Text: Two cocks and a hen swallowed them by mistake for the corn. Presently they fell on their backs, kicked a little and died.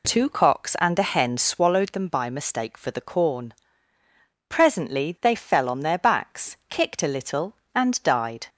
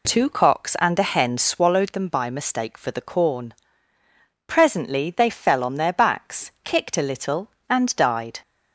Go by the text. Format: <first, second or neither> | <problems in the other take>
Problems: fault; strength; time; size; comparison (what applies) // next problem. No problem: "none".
neither | none